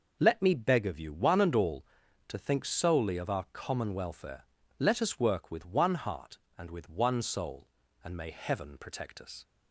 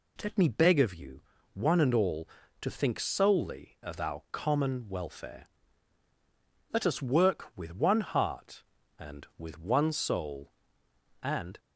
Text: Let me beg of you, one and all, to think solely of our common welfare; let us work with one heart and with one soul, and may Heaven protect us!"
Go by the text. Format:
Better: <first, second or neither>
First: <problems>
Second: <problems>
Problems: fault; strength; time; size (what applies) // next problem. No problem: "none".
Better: first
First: none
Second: stops before "may Heaven protect us"; at 11.5 s